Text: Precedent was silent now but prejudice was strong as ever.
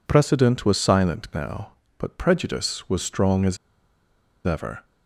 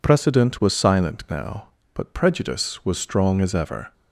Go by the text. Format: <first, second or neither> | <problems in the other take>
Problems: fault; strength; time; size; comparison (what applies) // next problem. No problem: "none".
second | pauses between "as" and "ever"; noticeable; at 3.5 s; 0.89 s long